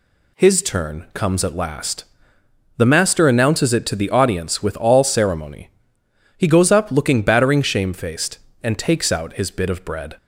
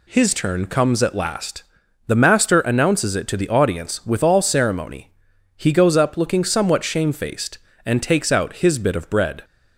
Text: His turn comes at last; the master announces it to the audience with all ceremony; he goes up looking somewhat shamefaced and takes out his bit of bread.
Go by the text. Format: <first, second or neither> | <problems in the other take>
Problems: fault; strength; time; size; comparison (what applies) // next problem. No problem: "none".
second | says "battering" for "somewhat"; at 7.2 s